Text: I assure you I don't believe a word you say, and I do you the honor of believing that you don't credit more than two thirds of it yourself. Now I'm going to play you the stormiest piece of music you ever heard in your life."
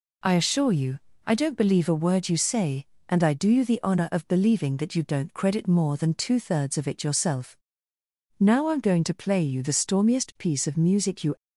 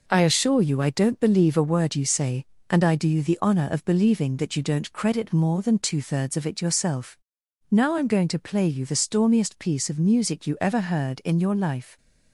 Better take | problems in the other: second | pauses between "you" and "I"; slight; at 0.9 s; 0.26 s long // stops before "ever heard in your life"; at 11.3 s

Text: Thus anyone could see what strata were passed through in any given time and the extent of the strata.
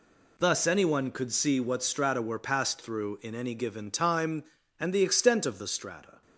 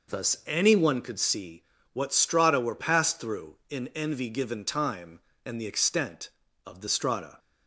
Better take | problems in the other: first | pauses between "see" and "what"; slight; at 1.6 s; 0.30 s long // says "envy" for "any"; at 3.9 s

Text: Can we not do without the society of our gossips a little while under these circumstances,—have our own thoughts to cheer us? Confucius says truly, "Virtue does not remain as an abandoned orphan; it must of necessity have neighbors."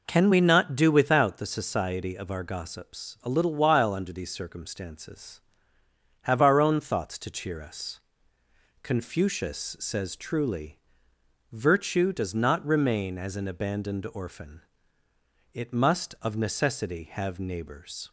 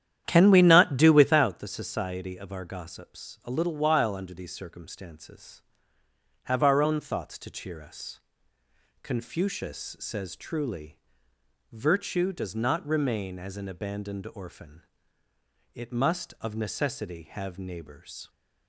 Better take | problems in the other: first | starts louder than the rest; strong; until 1.5 s; 10.5 dB

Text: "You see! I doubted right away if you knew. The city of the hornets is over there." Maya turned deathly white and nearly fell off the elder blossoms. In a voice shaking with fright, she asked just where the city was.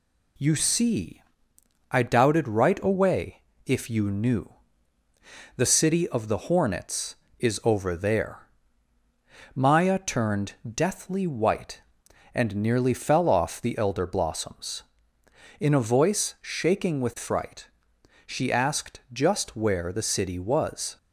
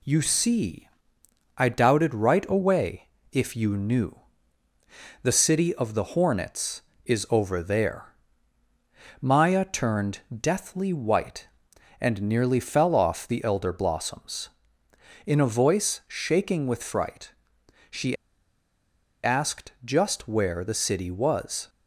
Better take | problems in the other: first | pauses between "away" and "if"; slight; at 3.0 s; 0.24 s long; slight in the first // pauses between "she" and "asked"; at 18.1 s; 1.0 s long

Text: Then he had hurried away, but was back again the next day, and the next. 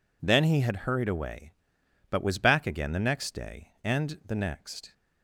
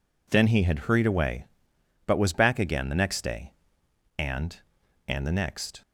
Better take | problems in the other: first | says "and" twice; at 5.0 s

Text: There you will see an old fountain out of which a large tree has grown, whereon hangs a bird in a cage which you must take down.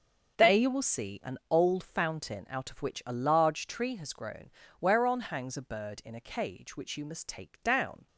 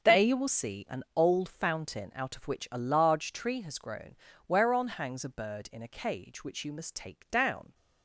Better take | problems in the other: neither | starts louder than the rest; the same in both

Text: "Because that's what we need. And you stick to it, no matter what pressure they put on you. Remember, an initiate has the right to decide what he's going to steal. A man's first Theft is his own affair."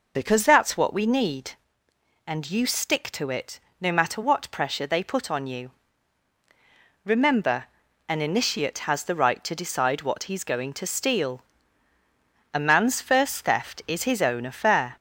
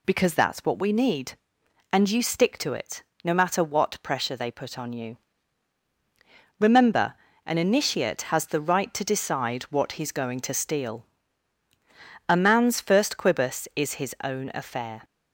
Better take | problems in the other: first | says "Quibus" for "Theft"; at 13.1 s

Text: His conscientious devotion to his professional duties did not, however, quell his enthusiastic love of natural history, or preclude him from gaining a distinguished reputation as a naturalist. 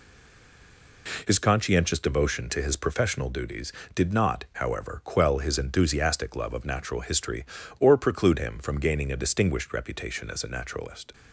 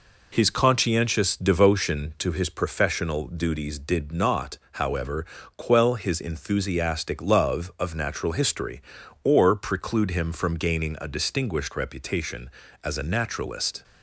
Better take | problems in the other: second | stays silent before the first word; until 1.0 s; 1.0 s long

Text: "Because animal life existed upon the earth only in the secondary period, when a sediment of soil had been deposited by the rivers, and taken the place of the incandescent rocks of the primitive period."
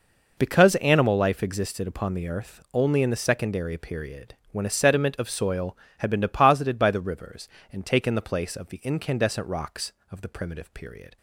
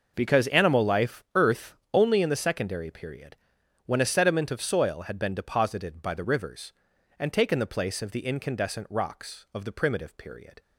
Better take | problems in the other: first | skips "existed upon the"; at 1.2 s // pauses between "earth" and "only"; slight; at 1.7 s; 0.18 s long

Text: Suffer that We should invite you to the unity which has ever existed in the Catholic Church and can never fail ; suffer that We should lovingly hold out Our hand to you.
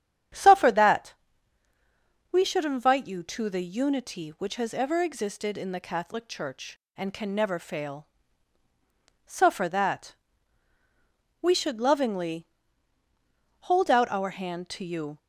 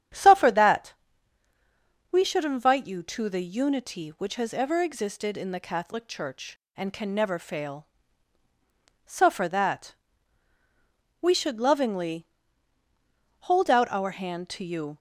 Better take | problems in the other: neither | starts louder than the rest; strong; the same in both // pauses between "that" and "We"; the same in both // pauses between "that" and "We"; strong; the same in both // pauses between "lovingly" and "hold"; the same in both

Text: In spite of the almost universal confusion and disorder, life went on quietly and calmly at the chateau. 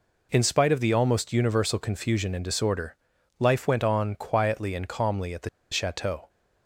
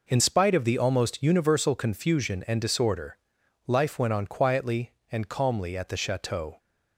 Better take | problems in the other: second | pauses between "the" and "chateau"; slight; at 5.4 s; 0.23 s long

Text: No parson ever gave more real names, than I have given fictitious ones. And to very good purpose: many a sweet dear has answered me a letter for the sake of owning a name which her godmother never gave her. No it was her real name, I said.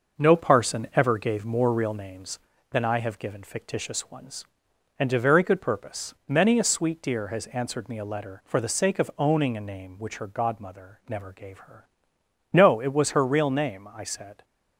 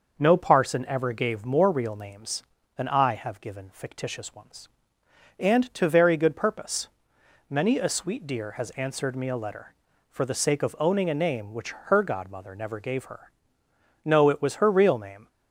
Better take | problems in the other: first | pauses between "which" and "her"; slight; at 11.7 s; 0.16 s long // stops before "I said"; at 15.2 s

